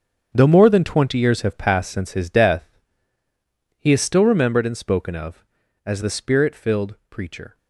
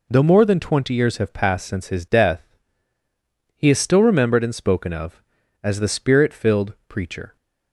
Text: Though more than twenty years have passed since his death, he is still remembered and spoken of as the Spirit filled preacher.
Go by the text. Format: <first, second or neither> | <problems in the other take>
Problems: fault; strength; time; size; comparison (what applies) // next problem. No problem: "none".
second | gets quieter; strong; throughout; 13 dB